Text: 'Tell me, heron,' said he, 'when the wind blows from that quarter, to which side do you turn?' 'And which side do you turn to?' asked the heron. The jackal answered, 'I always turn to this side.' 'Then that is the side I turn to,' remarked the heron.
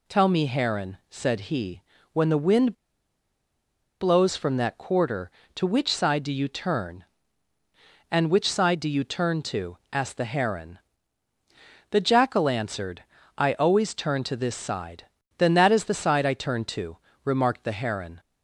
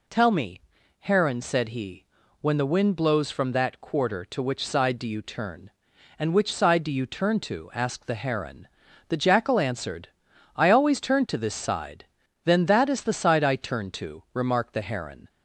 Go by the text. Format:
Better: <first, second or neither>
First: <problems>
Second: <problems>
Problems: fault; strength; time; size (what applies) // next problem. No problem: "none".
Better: second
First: pauses between "wind" and "blows"; strong; at 2.7 s; 1.2 s long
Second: none